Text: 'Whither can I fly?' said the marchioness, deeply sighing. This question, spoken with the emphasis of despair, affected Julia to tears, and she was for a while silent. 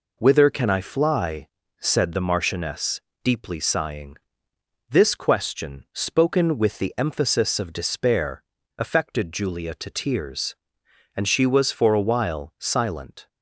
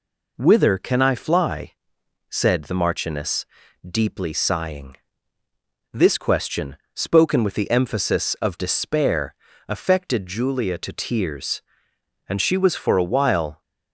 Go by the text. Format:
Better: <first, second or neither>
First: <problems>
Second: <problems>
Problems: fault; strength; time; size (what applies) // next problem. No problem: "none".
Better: first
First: none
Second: stops before "silent"; at 13.6 s